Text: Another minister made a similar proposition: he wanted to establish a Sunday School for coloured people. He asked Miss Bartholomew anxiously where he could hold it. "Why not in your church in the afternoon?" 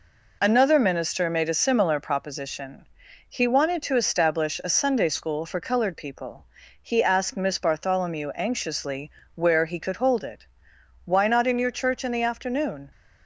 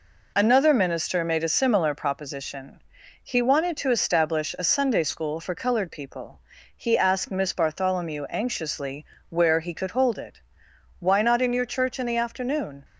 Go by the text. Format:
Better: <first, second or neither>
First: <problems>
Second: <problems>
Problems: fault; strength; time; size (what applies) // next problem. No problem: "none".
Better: neither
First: pauses between "anxiously" and "where"; slight; at 9.1 s; 0.24 s long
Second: pauses between "anxiously" and "where"; slight; at 9.0 s; 0.24 s long